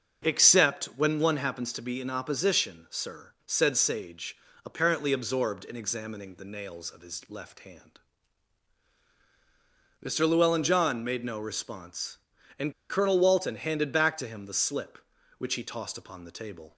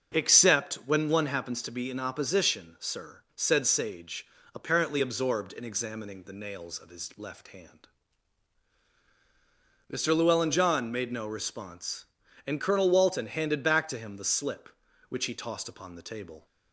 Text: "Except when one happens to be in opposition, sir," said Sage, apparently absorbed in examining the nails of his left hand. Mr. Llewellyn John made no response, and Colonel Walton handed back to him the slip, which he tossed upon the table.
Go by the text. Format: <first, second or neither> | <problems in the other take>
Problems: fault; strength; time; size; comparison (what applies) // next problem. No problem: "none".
second | starts louder than the rest; until 1.3 s; 6.5 dB; also in the second // pauses between "and" and "Colonel"; slight; at 12.7 s; 0.18 s long